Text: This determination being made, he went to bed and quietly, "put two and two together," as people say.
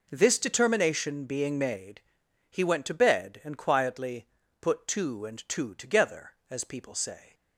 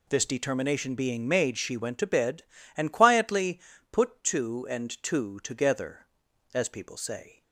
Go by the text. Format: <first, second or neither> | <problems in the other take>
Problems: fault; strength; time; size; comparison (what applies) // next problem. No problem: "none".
first | says "she" for "he"; at 1.5 s